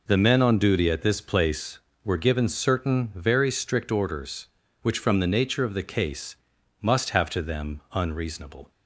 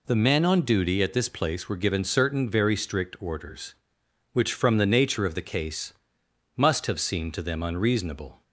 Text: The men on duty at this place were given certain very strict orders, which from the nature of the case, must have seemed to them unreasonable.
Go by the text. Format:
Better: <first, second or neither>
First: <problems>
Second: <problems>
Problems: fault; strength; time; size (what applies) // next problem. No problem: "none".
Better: second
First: skips "seemed"; at 7.2 s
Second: none